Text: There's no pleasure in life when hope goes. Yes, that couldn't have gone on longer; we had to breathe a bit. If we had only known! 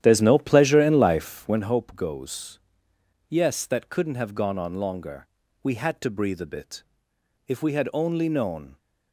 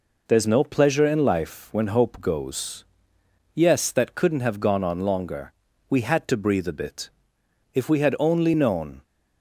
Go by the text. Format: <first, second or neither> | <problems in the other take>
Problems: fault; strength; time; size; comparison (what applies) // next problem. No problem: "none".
second | starts louder than the rest; strong; until 1.7 s; 11 dB